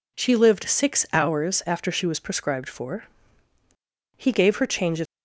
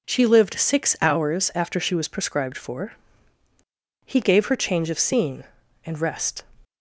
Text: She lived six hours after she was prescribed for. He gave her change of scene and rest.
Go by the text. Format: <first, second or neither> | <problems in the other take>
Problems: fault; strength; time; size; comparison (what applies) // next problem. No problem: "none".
second | stops before "scene and rest"; at 5.0 s